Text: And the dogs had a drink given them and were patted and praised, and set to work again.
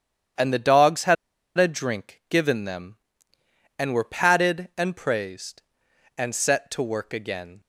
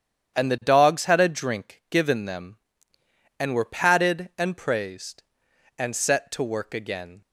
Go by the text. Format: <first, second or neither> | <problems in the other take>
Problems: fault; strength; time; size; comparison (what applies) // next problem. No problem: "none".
second | starts louder than the rest; strong; until 1.8 s; 9 dB; strong in the second // pauses between "had" and "a"; at 1.1 s; 0.42 s long